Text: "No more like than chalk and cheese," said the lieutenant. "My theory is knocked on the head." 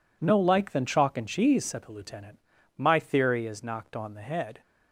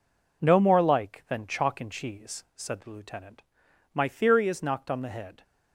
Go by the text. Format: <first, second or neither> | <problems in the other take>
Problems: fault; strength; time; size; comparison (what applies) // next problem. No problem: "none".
second | skips "more"; at 0.3 s